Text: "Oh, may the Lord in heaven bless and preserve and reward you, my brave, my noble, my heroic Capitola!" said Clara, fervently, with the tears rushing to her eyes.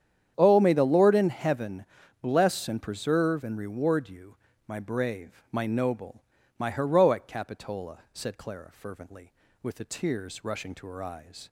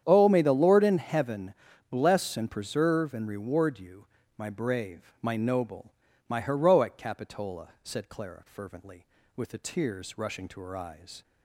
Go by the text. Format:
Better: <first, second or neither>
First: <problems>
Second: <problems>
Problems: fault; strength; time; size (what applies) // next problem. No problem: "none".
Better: neither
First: starts louder than the rest; strong; until 1.3 s; 9 dB // pauses between "heaven" and "bless"; slight; at 1.8 s; 0.36 s long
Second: starts louder than the rest; strong; until 1.0 s; 9 dB // pauses between "heaven" and "bless"; slight; at 1.5 s; 0.36 s long